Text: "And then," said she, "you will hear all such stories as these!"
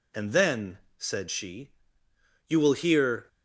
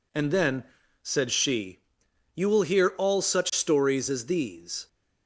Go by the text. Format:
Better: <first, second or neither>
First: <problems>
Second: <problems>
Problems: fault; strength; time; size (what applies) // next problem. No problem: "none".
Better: second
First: stops before "all such stories as these"; at 3.2 s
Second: none